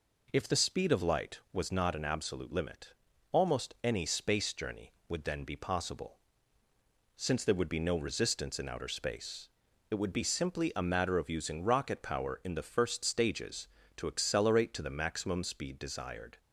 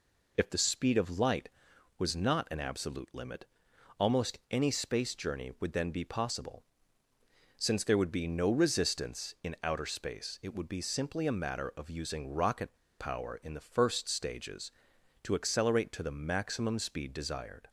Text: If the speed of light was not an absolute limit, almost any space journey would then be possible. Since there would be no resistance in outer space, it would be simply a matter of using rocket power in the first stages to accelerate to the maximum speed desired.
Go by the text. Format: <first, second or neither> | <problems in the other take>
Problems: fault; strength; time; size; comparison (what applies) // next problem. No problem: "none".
first | pauses between "rocket" and "power"; slight; at 12.7 s; 0.26 s long